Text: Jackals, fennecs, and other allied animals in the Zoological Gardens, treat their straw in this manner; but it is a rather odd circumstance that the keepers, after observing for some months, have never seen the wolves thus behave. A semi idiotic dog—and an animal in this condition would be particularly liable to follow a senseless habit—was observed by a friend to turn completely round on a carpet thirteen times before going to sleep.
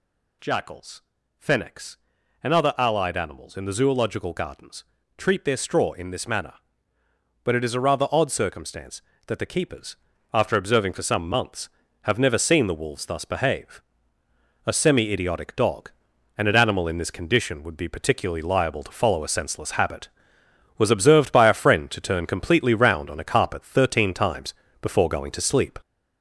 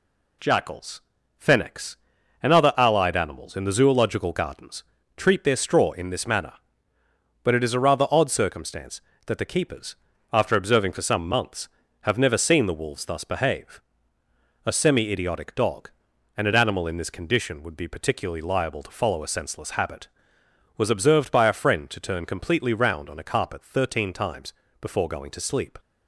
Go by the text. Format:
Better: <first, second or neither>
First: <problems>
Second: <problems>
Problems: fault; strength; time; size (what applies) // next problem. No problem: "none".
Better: second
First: gets louder; noticeable; throughout; 4.5 dB // pauses between "times" and "before"; slight; at 24.5 s; 0.26 s long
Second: pauses between "times" and "before"; slight; at 24.5 s; 0.26 s long